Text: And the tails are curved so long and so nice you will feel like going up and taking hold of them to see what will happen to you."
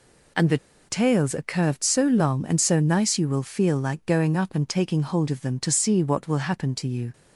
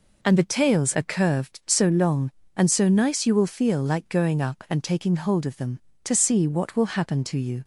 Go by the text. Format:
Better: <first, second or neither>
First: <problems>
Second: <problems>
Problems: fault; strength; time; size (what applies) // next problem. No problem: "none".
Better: second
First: pauses between "the" and "tails"; slight; at 0.5 s; 0.30 s long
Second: none